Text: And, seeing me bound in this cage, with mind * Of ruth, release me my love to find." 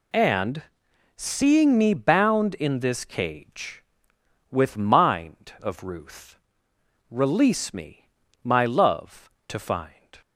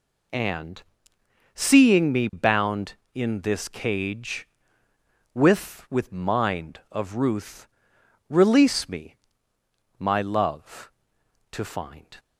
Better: first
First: pauses between "me" and "my"; slight; at 8.0 s; 0.34 s long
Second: says "with" twice; at 5.9 s // pauses between "me" and "my"; noticeable; at 9.1 s; 0.84 s long

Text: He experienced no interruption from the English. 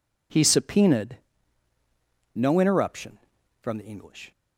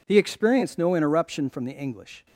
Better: second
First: says "subpoenaed" for "experienced"; at 0.4 s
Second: none

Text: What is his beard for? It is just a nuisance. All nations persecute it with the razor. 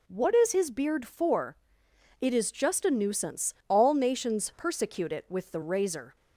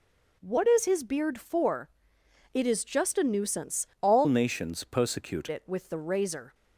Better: first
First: none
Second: changes voice from "nations" to "persecute"; from 4.2 to 5.4 s; 1.2 s long

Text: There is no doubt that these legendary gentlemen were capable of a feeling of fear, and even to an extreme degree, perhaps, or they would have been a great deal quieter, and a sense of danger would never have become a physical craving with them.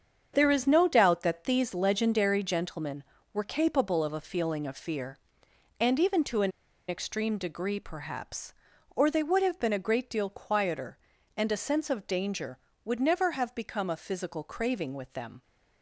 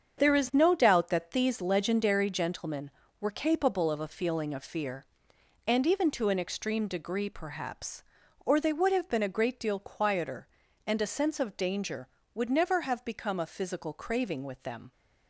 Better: second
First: starts louder than the rest; strong; until 1.3 s; 7 dB // pauses between "an" and "extreme"; at 6.5 s; 0.38 s long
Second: starts louder than the rest; strong; until 1.2 s; 7 dB

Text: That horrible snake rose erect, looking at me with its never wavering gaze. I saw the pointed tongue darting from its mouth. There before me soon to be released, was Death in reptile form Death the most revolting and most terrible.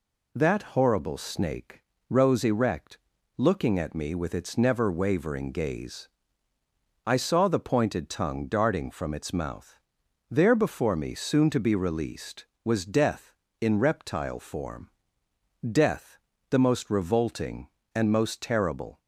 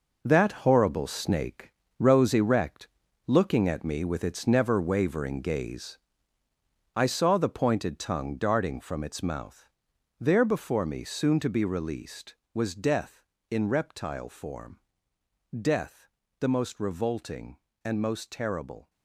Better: first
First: pauses between "snake" and "rose"; slight; at 1.8 s; 0.26 s long // pauses between "form" and "Death"; noticeable; at 14.9 s; 0.80 s long // pauses between "Death" and "the"; slight; at 16.1 s; 0.32 s long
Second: gets quieter; strong; throughout; 9.5 dB // pauses between "snake" and "rose"; slight; at 1.7 s; 0.26 s long // pauses between "form" and "Death"; noticeable; at 14.7 s; 0.80 s long // pauses between "Death" and "the"; slight; at 16.0 s; 0.32 s long

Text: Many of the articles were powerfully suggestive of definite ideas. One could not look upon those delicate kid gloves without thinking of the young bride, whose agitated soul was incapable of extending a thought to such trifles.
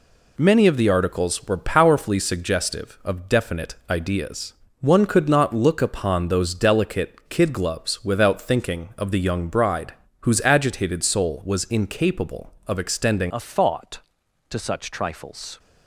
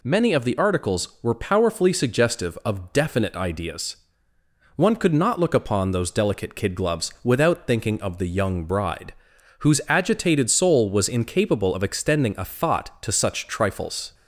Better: second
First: changes voice at "a"; from 13.3 s on; 2.2 s long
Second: none

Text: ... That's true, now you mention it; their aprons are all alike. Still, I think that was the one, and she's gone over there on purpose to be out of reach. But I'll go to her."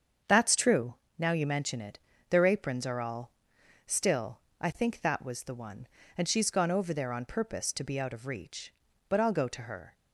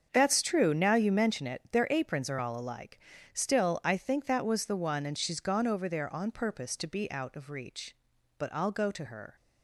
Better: second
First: starts louder than the rest; until 1.4 s; 7 dB // skips "alike"; at 3.5 s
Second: starts louder than the rest; strong; until 1.1 s; 7 dB

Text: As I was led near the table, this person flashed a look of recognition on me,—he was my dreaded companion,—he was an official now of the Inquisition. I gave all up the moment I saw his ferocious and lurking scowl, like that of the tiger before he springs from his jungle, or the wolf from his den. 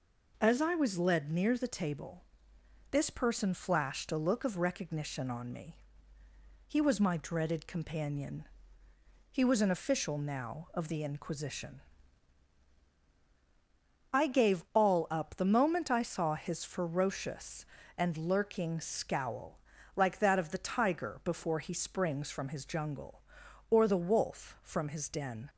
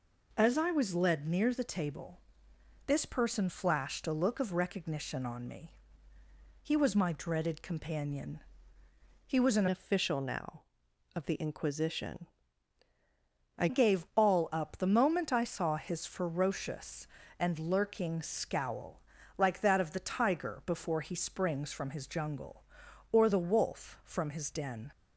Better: first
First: none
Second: changes voice from "official" to "I"; from 9.6 to 13.6 s; 4.0 s long

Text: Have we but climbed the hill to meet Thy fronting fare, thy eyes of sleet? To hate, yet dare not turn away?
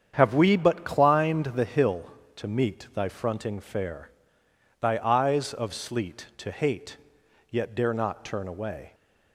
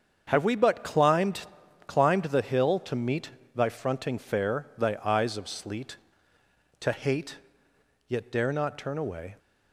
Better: first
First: starts louder than the rest; strong; until 1.1 s; 8 dB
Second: starts louder than the rest; strong; until 1.2 s; 7.5 dB // says "climbed" twice; at 1.8 s // pauses between "meet" and "Thy"; slight; at 3.3 s; 0.24 s long

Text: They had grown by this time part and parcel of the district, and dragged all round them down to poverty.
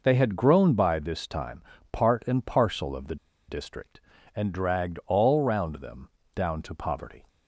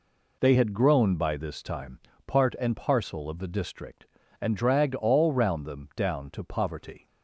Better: second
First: pauses between "time" and "part"; slight; at 1.6 s; 0.30 s long // pauses between "the" and "district"; slight; at 3.1 s; 0.33 s long // pauses between "them" and "down"; slight; at 6.0 s; 0.24 s long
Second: pauses between "time" and "part"; slight; at 1.9 s; 0.26 s long

